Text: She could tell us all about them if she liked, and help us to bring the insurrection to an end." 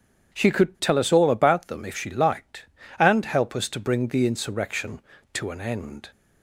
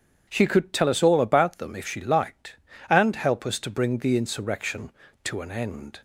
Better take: neither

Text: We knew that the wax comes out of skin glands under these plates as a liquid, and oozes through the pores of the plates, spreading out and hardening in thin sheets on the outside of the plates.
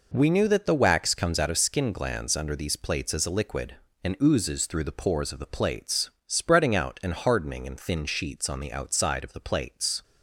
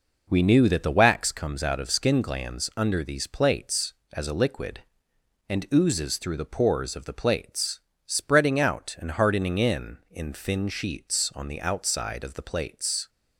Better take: first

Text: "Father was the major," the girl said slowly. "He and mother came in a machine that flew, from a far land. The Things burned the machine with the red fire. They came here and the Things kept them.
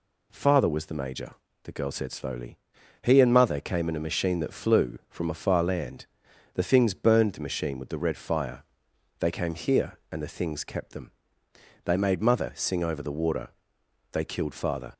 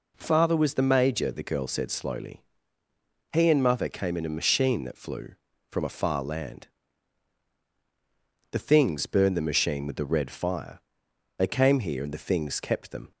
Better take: second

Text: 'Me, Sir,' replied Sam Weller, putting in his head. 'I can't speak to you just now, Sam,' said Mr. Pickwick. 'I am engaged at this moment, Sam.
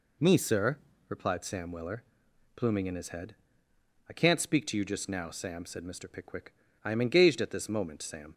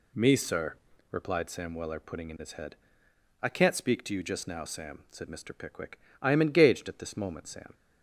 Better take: second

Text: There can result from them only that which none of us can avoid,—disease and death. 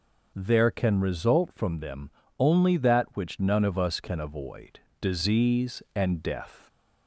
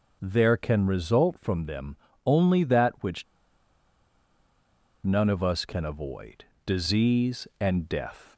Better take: first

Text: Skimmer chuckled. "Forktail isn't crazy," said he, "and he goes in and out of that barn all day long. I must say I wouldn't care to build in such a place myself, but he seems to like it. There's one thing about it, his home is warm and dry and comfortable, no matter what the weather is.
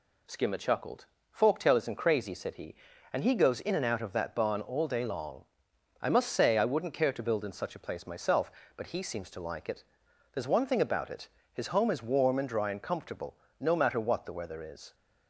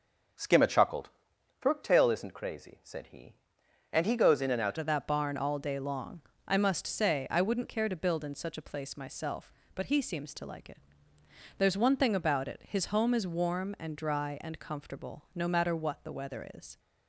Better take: first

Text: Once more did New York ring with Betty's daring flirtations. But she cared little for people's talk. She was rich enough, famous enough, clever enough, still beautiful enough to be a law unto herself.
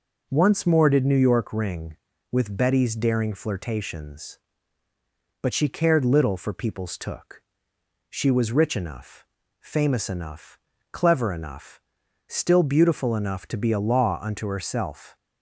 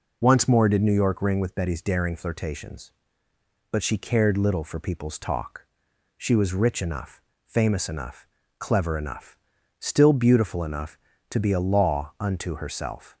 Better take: second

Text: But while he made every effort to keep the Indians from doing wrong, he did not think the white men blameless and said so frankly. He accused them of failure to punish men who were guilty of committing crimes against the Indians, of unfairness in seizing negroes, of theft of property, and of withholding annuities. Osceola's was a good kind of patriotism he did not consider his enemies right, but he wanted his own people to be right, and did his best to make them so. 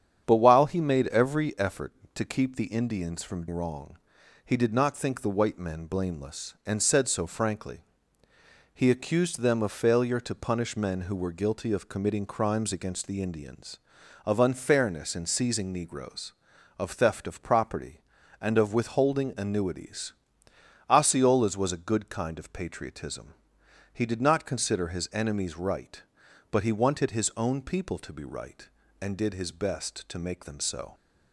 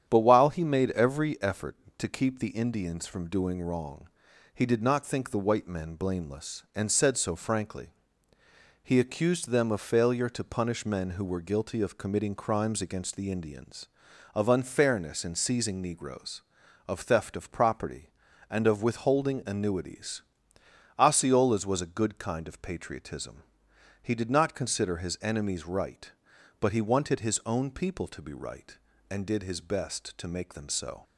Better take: second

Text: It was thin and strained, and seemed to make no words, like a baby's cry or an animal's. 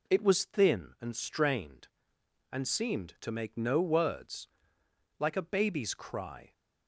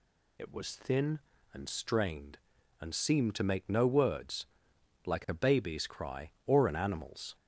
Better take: second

